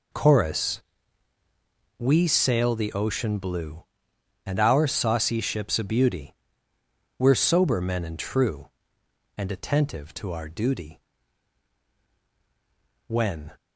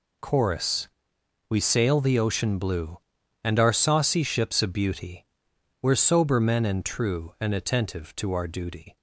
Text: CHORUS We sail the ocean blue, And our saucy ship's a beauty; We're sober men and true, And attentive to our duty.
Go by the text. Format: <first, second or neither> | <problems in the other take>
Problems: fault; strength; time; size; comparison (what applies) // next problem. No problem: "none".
second | pauses between "CHORUS" and "We"; at 0.8 s; 1.1 s long; noticeable in the second // goes on to say "When"; slight; from 13.0 s on; 0.44 s long